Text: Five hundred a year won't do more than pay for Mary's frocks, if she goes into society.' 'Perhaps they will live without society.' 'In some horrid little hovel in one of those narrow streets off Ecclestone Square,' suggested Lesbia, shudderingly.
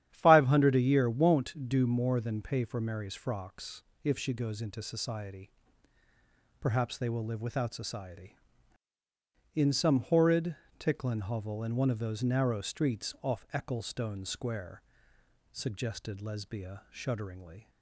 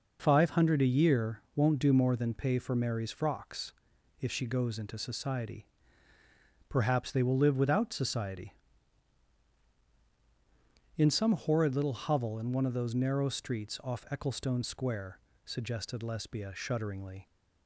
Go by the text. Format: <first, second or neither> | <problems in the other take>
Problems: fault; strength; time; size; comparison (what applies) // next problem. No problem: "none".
second | starts louder than the rest; strong; until 1.1 s; 10.5 dB // says "ticklin" for "little"; at 10.7 s